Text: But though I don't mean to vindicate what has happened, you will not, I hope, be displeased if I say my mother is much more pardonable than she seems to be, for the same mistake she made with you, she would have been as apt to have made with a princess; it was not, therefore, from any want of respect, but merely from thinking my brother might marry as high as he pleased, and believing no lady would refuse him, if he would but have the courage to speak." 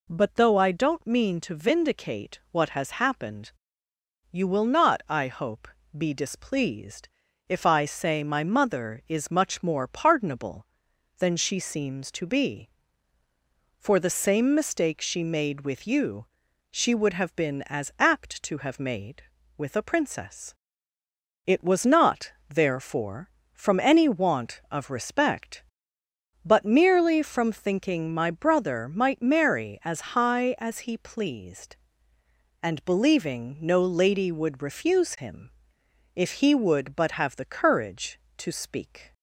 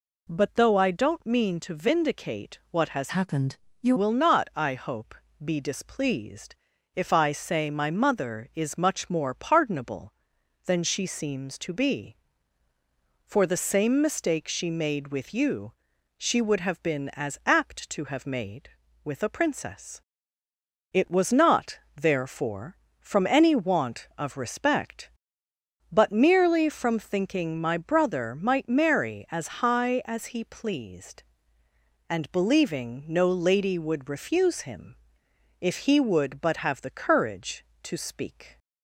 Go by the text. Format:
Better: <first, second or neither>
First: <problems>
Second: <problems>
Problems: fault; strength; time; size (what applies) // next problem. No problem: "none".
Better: first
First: pauses between "displeased" and "if"; at 7.0 s; 0.42 s long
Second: changes voice from "happened" to "you"; from 3.0 to 3.9 s; 0.9 s long // pauses between "displeased" and "if"; at 6.5 s; 0.42 s long